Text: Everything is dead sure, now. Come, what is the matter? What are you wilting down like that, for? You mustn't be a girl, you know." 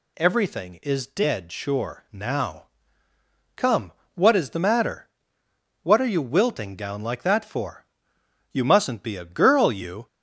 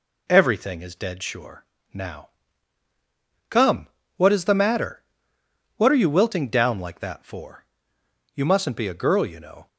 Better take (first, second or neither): second